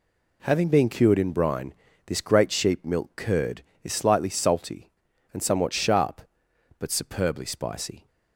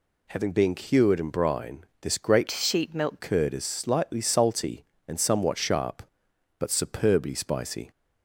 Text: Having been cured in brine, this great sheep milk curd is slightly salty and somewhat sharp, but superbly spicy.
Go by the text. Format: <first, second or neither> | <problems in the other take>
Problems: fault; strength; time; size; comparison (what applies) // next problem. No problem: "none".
first | changes voice from "sheep" to "milk"; from 2.5 to 3.1 s; 0.6 s long